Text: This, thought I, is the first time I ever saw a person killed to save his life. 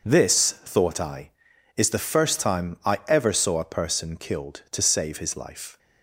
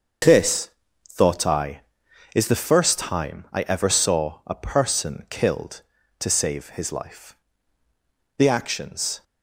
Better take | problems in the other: first | starts louder than the rest; until 1.6 s; 6.5 dB // goes on to say "The actions"; noticeable; from 8.3 s on; 0.86 s long

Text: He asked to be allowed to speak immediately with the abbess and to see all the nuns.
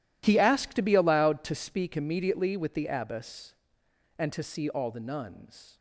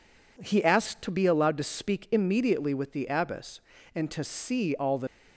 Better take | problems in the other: first | stops before "nuns"; at 5.0 s

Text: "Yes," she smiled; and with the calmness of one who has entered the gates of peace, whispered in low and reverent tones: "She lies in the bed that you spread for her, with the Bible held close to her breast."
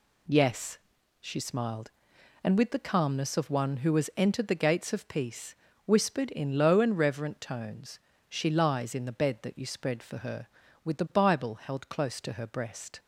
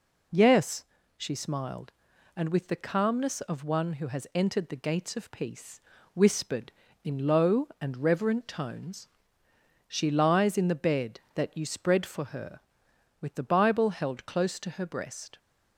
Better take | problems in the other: neither | none

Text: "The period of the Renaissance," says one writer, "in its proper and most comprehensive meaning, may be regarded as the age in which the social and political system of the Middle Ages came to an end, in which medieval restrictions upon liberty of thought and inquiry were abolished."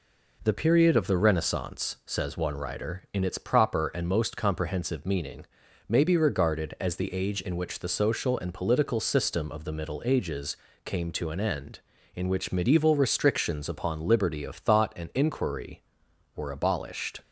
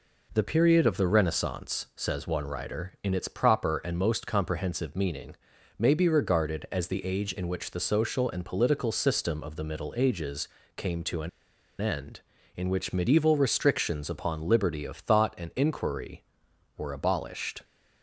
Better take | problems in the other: first | pauses between "Ages" and "came"; slight; at 10.4 s; 0.30 s long; slight in the first // pauses between "an" and "end"; noticeable; at 11.2 s; 0.51 s long

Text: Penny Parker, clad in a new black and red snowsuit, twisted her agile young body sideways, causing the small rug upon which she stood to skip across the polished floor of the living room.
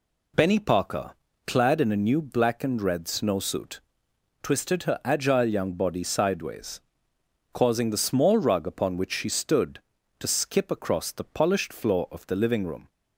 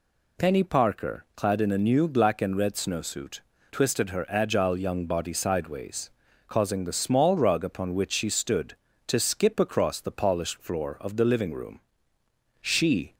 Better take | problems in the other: first | goes on to say "She"; from 12.5 s on; 0.54 s long

